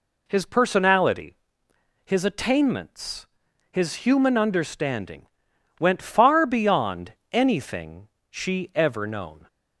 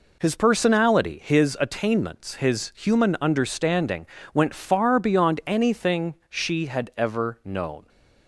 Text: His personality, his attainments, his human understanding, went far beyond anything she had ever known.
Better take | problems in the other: second | pauses between "beyond" and "anything"; slight; at 7.1 s; 0.18 s long // pauses between "anything" and "she"; slight; at 8.0 s; 0.22 s long // skips "had"; at 8.7 s

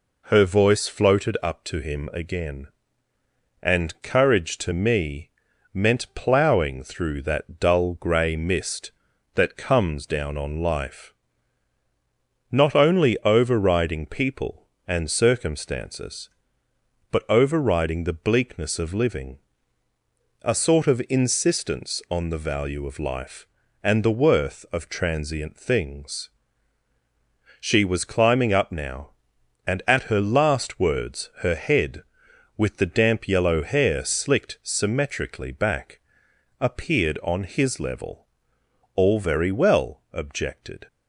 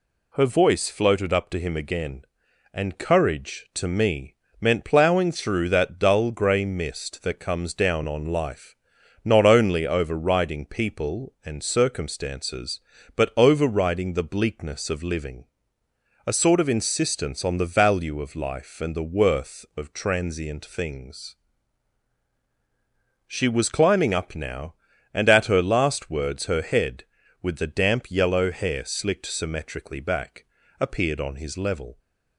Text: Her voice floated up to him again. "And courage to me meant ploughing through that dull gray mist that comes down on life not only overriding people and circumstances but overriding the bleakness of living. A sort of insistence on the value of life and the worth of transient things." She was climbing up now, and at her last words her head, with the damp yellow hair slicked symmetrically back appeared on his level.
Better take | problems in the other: second | pauses between "me" and "meant"; at 5.2 s; 0.42 s long; slight in the second // pauses between "life" and "not"; strong; at 11.1 s; 1.3 s long; noticeable in the second // pauses between "back" and "appeared"; noticeable; at 35.9 s; 0.60 s long; slight in the second // goes on to say "All very well objected"; strong; from 38.9 s on; 1.9 s long

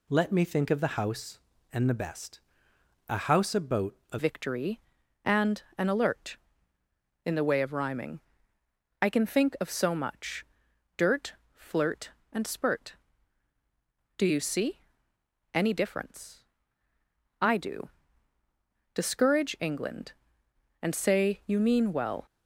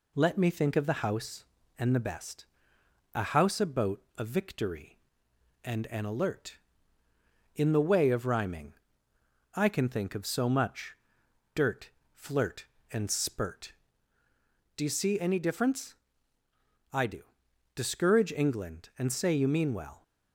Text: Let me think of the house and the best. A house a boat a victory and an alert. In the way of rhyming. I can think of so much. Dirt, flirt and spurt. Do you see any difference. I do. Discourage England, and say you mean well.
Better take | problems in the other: second | pauses between "boat" and "a"; slight; at 3.9 s; 0.16 s long; slight in the second // changes voice at "victory"; from 4.1 s on; 18.1 s long // pauses between "and" and "an"; slight; at 5.6 s; 0.16 s long // pauses between "see" and "any"; noticeable; at 14.7 s; 0.76 s long

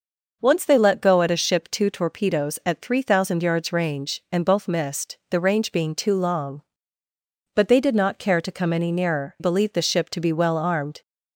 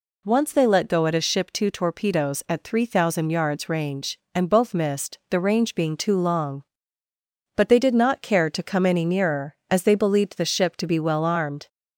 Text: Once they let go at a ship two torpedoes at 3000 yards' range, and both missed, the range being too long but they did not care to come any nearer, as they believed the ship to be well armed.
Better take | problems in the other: second | skips "as they"; at 9.3 s

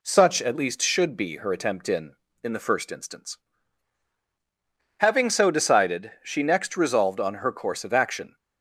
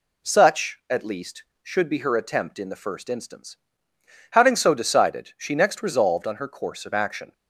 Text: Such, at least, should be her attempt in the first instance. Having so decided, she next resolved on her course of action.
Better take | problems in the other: second | says "in" twice; at 2.4 s

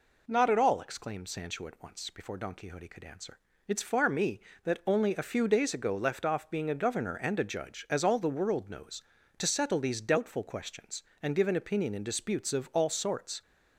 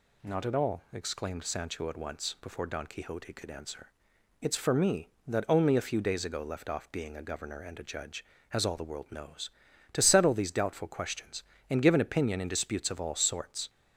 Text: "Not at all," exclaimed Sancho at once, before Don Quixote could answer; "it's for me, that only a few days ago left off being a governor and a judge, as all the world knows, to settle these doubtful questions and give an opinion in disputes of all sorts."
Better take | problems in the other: second | says "far" for "for"; at 3.8 s

